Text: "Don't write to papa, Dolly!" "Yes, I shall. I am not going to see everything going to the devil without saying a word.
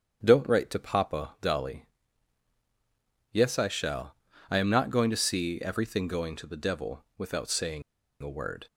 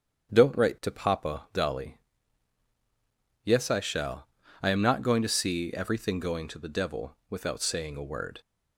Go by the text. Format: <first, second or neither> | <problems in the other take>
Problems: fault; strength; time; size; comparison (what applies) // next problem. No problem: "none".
second | starts louder than the rest; strong; until 1.2 s; 7.5 dB; strong in the second // pauses between "saying" and "a"; at 7.8 s; 0.40 s long